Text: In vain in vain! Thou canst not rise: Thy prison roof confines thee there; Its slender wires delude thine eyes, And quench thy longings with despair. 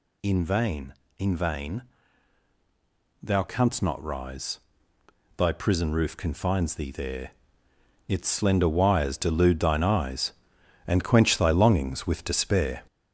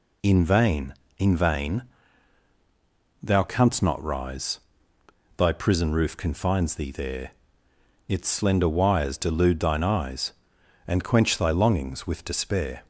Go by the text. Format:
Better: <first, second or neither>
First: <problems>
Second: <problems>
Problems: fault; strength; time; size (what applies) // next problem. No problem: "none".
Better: second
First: gets louder; noticeable; throughout; 5.5 dB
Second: none